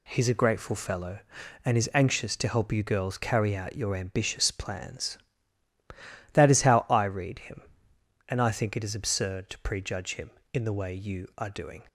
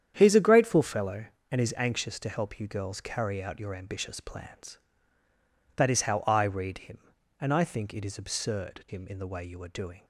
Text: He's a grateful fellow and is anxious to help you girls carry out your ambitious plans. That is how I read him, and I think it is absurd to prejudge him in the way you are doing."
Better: first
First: none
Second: starts louder than the rest; strong; until 1.1 s; 9 dB // skips "to prejudge"; at 8.8 s

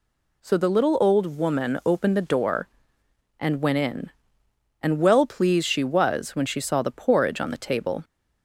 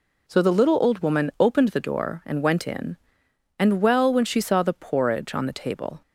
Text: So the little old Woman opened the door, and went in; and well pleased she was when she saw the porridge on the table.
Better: first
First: none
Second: skips "pleased she was"; at 4.1 s

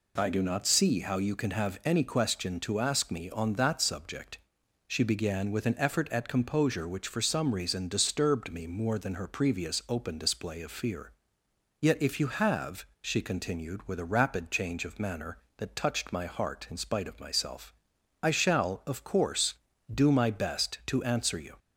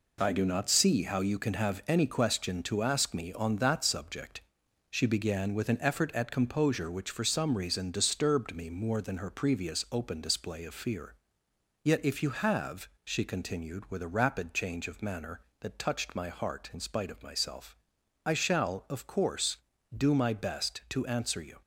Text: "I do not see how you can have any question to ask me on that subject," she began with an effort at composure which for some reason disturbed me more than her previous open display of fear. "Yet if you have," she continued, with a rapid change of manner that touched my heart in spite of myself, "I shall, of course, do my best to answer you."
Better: first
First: none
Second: gets quieter; throughout; 6.5 dB

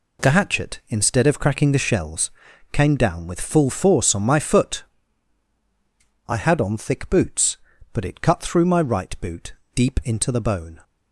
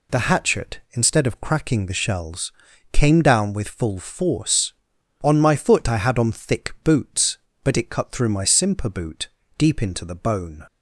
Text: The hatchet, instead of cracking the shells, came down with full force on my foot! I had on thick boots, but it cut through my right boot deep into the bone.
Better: first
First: pauses between "boot" and "deep"; slight; at 9.5 s; 0.22 s long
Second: says "simper" for "right"; at 8.4 s // pauses between "boot" and "deep"; slight; at 9.2 s; 0.29 s long

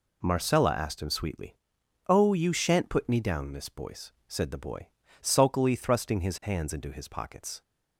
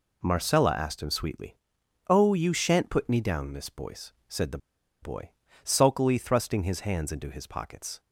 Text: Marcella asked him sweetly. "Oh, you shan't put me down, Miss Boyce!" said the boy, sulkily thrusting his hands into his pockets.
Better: first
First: none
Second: pauses between "the" and "boy"; at 4.5 s; 0.44 s long

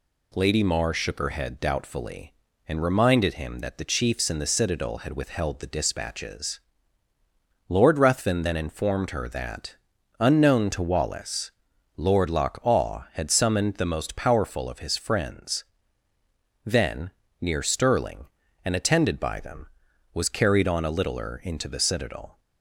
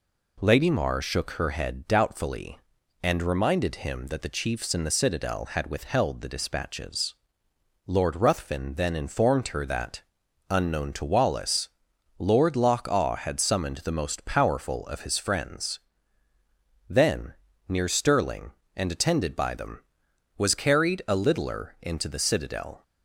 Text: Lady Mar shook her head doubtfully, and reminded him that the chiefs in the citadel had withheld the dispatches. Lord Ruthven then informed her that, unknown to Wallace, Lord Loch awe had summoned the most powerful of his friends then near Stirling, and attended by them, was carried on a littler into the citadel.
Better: first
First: pauses between "friends" and "then"; at 15.6 s; 1.0 s long // pauses between "then" and "near"; slight; at 17.1 s; 0.30 s long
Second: pauses between "friends" and "then"; at 15.7 s; 1.1 s long // pauses between "then" and "near"; slight; at 17.3 s; 0.34 s long // skips "on"; at 21.0 s

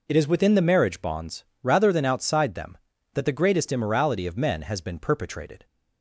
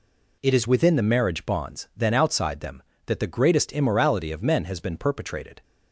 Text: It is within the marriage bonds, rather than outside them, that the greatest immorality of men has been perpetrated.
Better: first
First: none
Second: skips "rather"; at 1.9 s

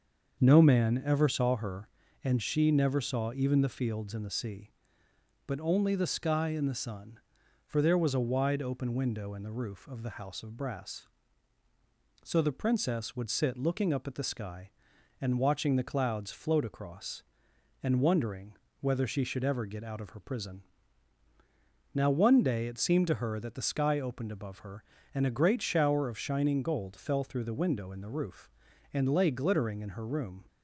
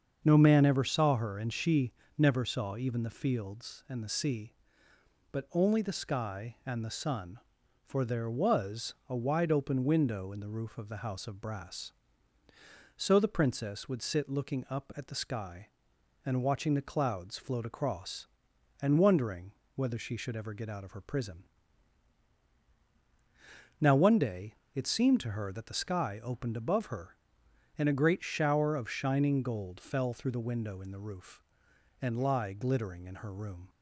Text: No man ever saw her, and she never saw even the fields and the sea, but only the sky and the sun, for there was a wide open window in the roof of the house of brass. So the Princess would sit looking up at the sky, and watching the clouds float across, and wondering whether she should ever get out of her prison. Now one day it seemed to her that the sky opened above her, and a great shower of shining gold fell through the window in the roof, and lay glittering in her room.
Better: first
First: starts louder than the rest; until 1.4 s; 6.5 dB // pauses between "wondering" and "whether"; slight; at 18.5 s; 0.26 s long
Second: starts louder than the rest; until 1.2 s; 7 dB // pauses between "she" and "never"; slight; at 1.9 s; 0.24 s long // pauses between "wondering" and "whether"; slight; at 19.5 s; 0.22 s long // pauses between "day" and "it"; slight; at 24.5 s; 0.20 s long // says "lie" for "lay"; at 32.2 s

